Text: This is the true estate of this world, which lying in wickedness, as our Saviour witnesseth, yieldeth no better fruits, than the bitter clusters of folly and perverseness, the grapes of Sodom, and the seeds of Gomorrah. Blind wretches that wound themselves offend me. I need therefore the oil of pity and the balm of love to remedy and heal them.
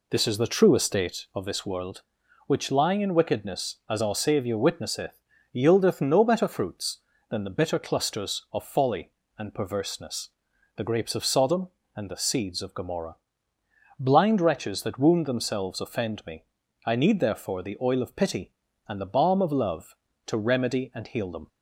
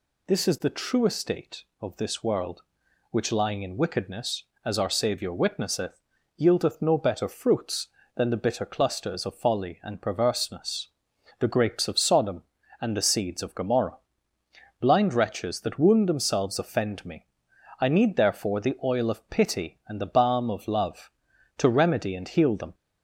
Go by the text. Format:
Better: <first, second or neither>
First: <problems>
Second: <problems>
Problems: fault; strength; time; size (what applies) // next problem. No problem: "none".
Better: second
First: starts louder than the rest; slight; until 1.5 s; 2.5 dB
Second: none